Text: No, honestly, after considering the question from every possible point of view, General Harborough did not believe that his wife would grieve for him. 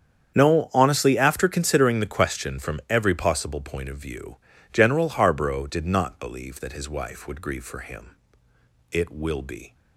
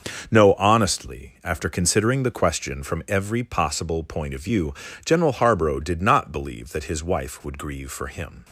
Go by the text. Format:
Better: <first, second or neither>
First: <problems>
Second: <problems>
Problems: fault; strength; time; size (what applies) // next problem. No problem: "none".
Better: second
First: starts louder than the rest; strong; until 1.4 s; 8 dB // goes on to say "It will be"; noticeable; from 8.9 s on; 0.84 s long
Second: starts louder than the rest; noticeable; until 1.3 s; 6 dB